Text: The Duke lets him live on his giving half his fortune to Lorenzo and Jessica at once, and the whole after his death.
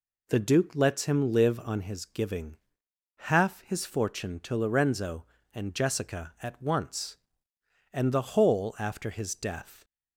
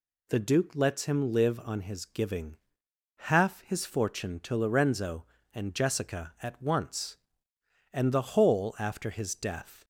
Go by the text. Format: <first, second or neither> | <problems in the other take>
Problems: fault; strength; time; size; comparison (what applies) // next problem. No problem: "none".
second | starts louder than the rest; slight; until 2.0 s; 3 dB // pauses between "giving" and "half"; noticeable; at 2.5 s; 0.74 s long; noticeable in the second